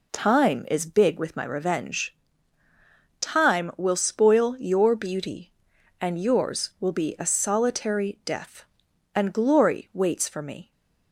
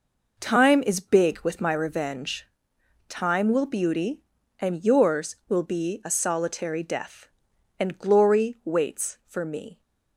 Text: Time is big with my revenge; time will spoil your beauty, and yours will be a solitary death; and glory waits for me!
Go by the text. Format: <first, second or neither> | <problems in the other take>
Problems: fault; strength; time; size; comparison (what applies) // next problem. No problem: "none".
first | skips "spoil your"; at 3.6 s